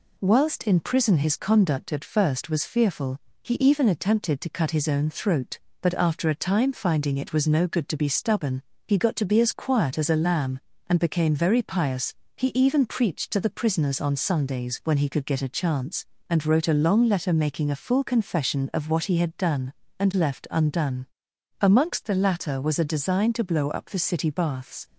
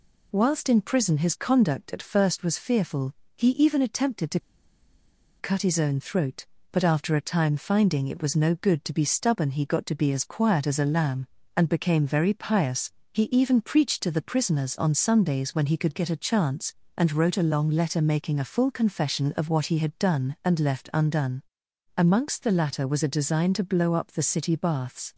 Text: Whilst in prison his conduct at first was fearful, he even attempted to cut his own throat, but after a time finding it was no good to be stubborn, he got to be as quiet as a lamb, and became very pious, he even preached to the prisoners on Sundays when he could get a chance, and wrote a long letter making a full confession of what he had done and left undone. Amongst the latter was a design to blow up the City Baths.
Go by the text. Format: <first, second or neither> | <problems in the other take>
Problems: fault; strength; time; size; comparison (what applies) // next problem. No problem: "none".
first | pauses between "to" and "cut"; at 4.4 s; 0.99 s long